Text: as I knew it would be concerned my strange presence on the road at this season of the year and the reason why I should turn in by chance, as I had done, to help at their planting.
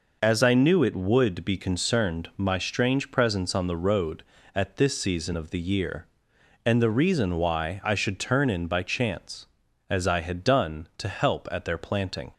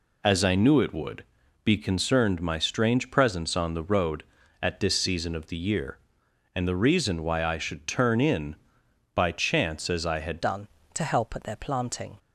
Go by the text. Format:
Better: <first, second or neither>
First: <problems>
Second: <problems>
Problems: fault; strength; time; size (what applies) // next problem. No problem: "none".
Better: first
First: none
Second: pauses between "would" and "be"; at 1.2 s; 0.40 s long // changes voice at "done"; from 10.4 s on; 1.7 s long